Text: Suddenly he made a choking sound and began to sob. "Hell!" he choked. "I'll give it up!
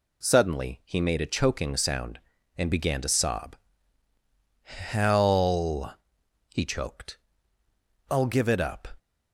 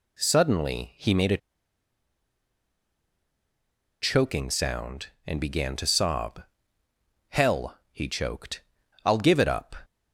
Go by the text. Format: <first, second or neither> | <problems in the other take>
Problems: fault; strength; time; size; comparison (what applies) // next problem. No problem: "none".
first | pauses between "a" and "choking"; strong; at 1.3 s; 2.6 s long